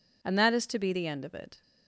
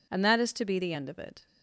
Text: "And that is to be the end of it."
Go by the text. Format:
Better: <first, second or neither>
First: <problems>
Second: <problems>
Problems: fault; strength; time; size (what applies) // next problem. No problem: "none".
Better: neither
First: none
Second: none